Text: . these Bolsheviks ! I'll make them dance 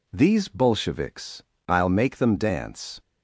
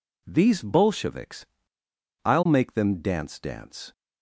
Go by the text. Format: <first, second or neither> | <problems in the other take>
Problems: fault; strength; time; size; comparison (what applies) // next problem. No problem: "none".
first | says "dance" twice; at 3.3 s